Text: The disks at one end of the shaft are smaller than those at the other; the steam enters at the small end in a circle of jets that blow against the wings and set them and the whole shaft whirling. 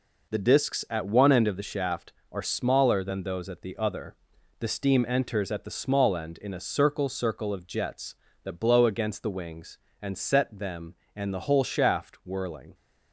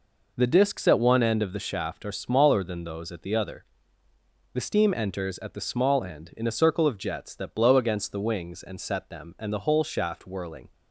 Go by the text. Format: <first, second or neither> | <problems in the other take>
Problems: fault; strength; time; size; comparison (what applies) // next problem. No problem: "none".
second | says "circle" twice; at 7.0 s